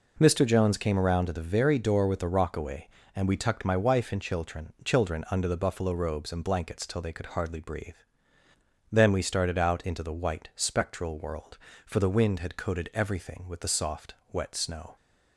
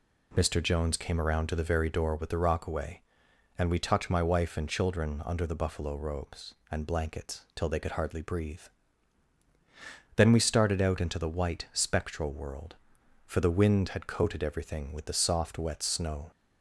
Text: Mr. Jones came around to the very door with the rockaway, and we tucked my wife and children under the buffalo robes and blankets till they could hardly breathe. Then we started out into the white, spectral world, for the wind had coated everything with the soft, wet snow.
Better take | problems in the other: second | says "children" twice; at 4.8 s

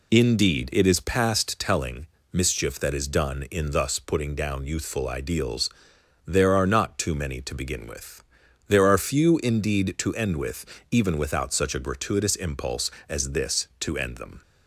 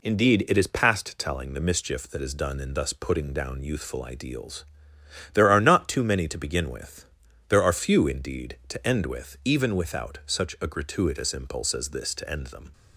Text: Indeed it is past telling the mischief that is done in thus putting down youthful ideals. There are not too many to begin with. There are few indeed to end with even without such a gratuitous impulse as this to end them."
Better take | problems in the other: second | skips "the"; at 2.2 s // pauses between "with" and "even"; slight; at 10.6 s; 0.24 s long

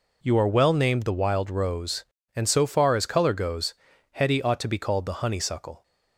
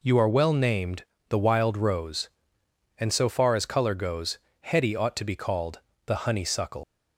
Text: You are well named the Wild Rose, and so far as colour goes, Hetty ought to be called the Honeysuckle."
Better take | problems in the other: first | pauses between "named" and "the"; slight; at 1.0 s; 0.26 s long // pauses between "called" and "the"; slight; at 5.7 s; 0.28 s long // leaves "Honeysuckle" unfinished; at 6.8 s; 140 ms

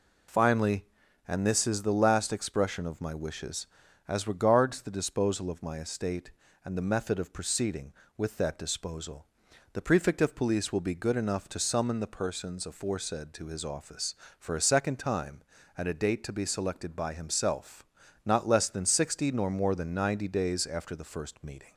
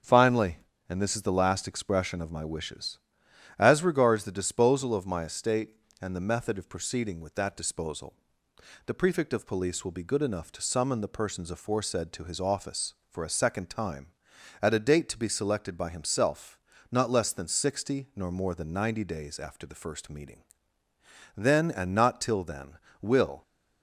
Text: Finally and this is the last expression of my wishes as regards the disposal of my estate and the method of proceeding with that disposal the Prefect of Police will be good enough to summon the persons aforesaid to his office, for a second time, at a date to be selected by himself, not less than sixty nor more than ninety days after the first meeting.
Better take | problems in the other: first | starts louder than the rest; until 1.3 s; 6.5 dB // pauses between "disposal" and "the"; noticeable; at 8.1 s; 0.72 s long; noticeable in the first // goes on to say "Then and not till then will"; strong; from 21.3 s on; 2.0 s long

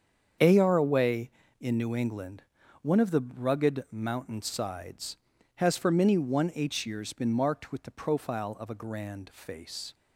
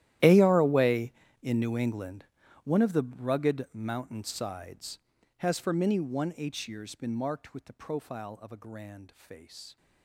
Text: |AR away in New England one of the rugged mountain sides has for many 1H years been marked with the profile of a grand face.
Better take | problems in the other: first | gets quieter; strong; throughout; 21 dB // starts louder than the rest; strong; until 1.5 s; 13 dB; strong in the first // pauses between "England" and "one"; at 2.2 s; 0.40 s long; also in the first

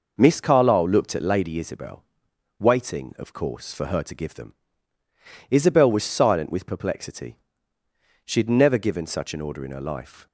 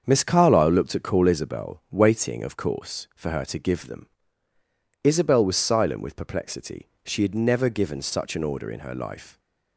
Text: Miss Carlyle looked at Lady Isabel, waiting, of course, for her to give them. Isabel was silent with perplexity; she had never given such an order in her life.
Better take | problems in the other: first | starts louder than the rest; until 1.0 s; 7 dB // says "Call" for "Lady"; at 1.0 s

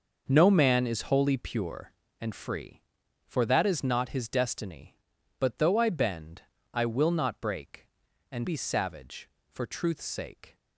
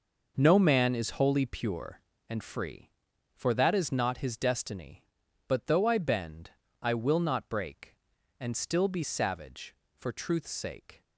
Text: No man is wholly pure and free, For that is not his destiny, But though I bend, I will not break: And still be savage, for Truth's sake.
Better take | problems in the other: second | starts louder than the rest; noticeable; until 1.2 s; 6 dB // skips "still"; at 8.4 s

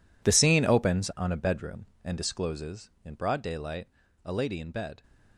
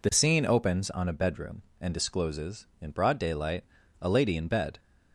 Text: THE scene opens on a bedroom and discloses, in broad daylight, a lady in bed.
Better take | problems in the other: second | gets quieter; strong; throughout; 15 dB

